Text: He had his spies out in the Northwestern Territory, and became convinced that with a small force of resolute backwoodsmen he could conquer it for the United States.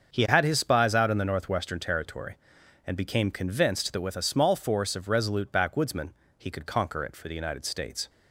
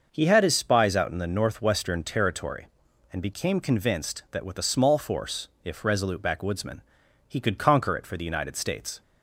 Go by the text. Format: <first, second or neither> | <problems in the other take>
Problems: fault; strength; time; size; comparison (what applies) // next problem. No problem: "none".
first | starts louder than the rest; until 1.1 s; 6 dB; also in the first // says "if" for "of"; at 5.6 s // pauses between "backwoodsmen" and "he"; noticeable; at 6.7 s; 0.48 s long; slight in the first